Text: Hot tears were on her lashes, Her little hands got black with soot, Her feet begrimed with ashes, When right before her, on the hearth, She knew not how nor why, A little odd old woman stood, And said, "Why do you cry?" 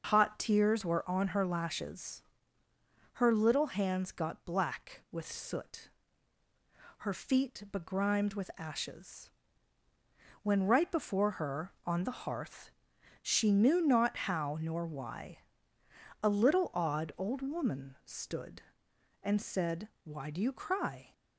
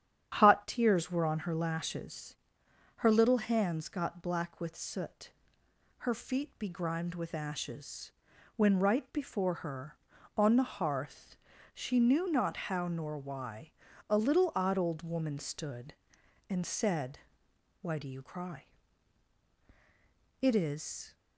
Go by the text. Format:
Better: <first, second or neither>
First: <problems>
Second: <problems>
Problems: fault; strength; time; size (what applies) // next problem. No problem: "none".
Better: first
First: starts louder than the rest; noticeable; until 1.1 s; 6 dB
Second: starts louder than the rest; strong; until 1.3 s; 9.5 dB // goes on to say "It is"; noticeable; from 20.4 s on; 0.74 s long